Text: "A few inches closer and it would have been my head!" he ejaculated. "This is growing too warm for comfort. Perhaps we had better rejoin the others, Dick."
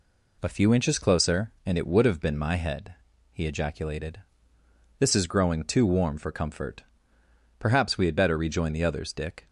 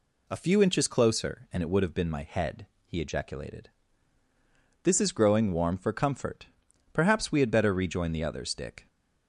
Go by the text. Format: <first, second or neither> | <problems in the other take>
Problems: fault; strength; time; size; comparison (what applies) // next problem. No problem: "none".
first | skips "too"; at 5.5 s